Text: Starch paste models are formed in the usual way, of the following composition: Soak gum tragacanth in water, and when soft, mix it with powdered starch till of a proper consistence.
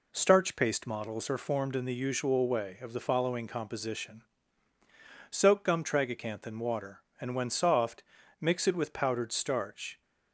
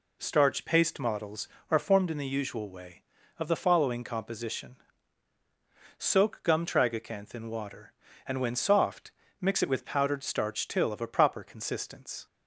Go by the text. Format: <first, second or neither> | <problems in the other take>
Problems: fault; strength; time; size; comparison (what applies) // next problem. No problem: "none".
second | stops before "till of a proper consistence"; at 10.0 s